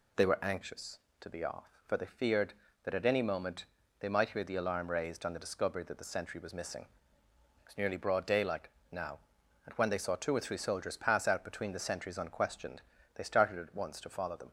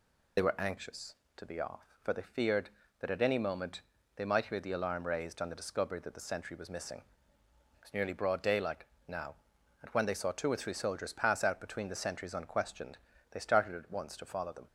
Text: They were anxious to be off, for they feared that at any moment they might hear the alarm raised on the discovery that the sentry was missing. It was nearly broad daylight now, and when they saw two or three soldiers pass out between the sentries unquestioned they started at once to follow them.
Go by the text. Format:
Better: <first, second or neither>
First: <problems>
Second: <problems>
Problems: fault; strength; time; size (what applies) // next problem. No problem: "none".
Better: first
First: pauses between "moment" and "they"; slight; at 3.6 s; 0.34 s long // pauses between "daylight" and "now"; slight; at 8.6 s; 0.24 s long // pauses between "unquestioned" and "they"; slight; at 12.8 s; 0.36 s long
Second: loses the start of "They"; at 0.3 s; 50 ms // pauses between "moment" and "they"; slight; at 3.8 s; 0.34 s long // pauses between "daylight" and "now"; slight; at 8.8 s; 0.24 s long // pauses between "unquestioned" and "they"; slight; at 12.9 s; 0.36 s long